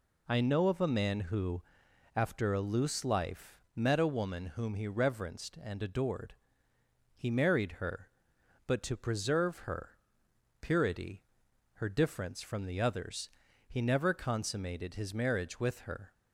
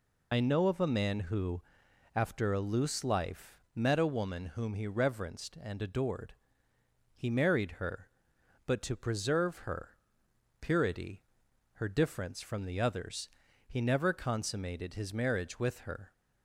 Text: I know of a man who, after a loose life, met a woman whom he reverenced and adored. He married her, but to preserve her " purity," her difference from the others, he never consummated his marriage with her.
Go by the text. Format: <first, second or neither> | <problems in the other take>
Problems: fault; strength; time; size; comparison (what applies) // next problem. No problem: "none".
first | loses the start of "I"; at 0.3 s; 50 ms